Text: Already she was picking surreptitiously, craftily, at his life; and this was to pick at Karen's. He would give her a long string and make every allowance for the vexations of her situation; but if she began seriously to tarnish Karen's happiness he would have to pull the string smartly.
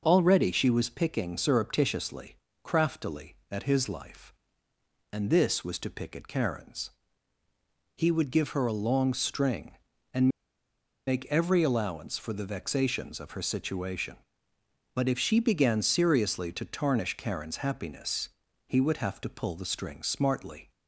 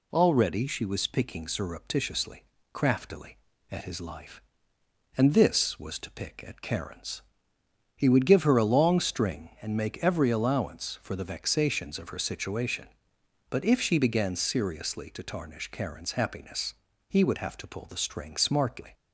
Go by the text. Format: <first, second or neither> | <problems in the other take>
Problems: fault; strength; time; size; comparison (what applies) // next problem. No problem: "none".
second | pauses between "and" and "make"; noticeable; at 10.2 s; 0.79 s long // pauses between "happiness" and "he"; slight; at 18.3 s; 0.36 s long; slight in the second